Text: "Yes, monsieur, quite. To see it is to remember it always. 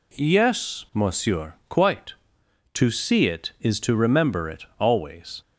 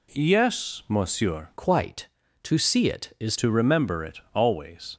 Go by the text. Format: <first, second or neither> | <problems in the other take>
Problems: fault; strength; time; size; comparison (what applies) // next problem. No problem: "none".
first | changes voice from "quite" to "is"; from 1.5 to 3.3 s; 1.8 s long // pauses between "it" and "always"; slight; at 4.1 s; 0.16 s long; slight in the first